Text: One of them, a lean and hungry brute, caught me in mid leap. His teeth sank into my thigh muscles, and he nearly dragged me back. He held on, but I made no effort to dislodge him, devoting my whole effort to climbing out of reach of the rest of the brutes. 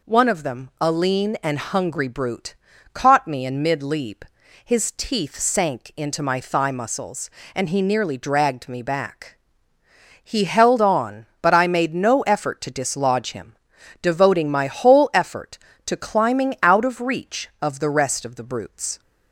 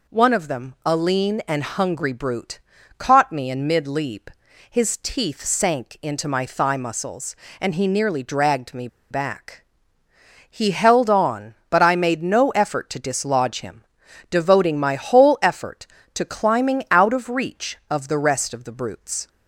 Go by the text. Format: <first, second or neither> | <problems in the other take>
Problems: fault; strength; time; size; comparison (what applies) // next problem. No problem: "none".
first | pauses between "me" and "back"; slight; at 8.8 s; 0.23 s long